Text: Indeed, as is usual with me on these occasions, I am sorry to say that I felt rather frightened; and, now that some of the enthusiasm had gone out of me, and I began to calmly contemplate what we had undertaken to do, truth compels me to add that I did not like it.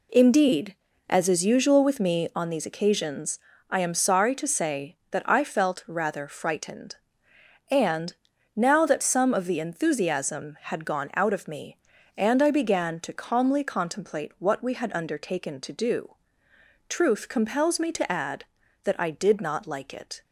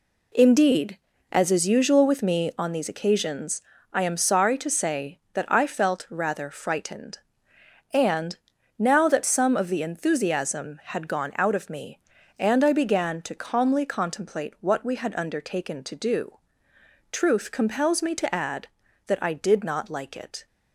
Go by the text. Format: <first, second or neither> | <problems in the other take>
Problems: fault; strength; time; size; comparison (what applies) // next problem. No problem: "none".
neither | none